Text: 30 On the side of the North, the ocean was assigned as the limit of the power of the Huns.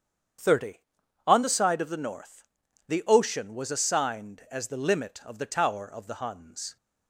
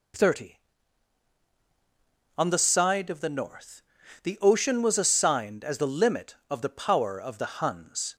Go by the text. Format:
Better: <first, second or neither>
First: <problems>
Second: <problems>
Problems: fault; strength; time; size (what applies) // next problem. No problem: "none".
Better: second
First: starts louder than the rest; strong; until 1.9 s; 8 dB // says "tower" for "power"; at 5.4 s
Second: none